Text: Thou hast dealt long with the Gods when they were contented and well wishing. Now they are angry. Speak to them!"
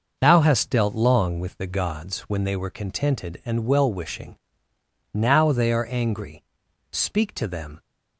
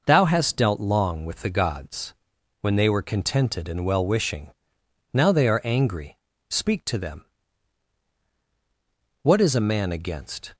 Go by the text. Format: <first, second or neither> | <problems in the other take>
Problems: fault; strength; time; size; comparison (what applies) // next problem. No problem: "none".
first | pauses between "Gods" and "when"; noticeable; at 2.1 s; 0.48 s long // goes on to say "What is a man against"; from 9.2 s on; 1.3 s long